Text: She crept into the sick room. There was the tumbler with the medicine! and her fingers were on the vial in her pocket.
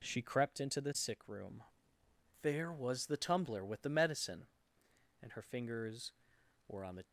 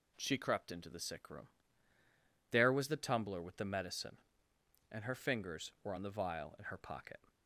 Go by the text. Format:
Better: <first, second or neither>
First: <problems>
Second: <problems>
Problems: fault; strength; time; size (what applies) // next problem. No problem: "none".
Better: second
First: stops before "vial in her pocket"; at 7.0 s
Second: none